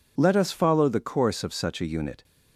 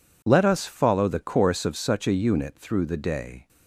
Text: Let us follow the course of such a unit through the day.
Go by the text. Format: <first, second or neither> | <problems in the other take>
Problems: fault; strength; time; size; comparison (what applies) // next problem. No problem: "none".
second | stops before "through the day"; at 2.2 s